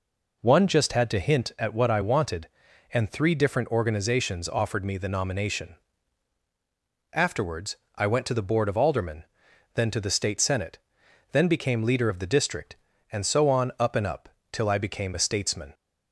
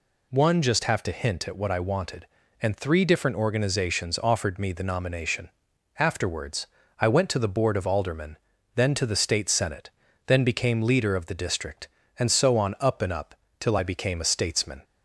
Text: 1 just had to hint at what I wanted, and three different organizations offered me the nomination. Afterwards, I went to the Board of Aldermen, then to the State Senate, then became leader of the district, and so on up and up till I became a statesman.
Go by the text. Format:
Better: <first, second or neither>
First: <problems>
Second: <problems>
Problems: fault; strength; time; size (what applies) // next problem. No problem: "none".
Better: first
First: pauses between "up" and "till"; slight; at 14.2 s; 0.24 s long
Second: says "have" for "had"; at 0.8 s // pauses between "up" and "till"; slight; at 13.3 s; 0.24 s long